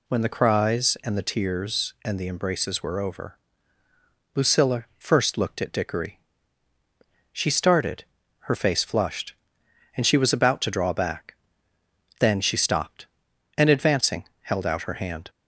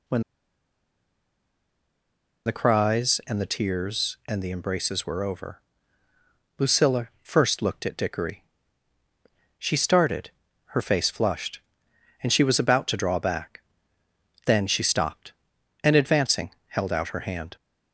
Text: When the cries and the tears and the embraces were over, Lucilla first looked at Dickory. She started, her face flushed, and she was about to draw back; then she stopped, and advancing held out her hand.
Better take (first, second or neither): first